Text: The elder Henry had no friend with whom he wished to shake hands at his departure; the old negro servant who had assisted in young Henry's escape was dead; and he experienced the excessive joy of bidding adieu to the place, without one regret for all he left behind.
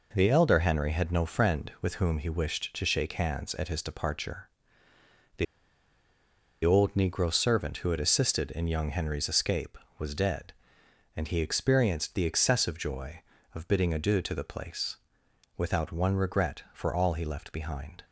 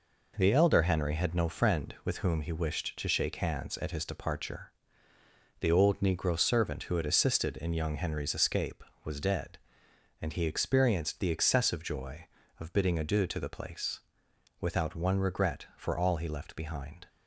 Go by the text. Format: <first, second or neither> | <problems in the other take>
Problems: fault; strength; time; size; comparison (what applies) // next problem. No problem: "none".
second | pauses between "the" and "old"; at 5.4 s; 1.1 s long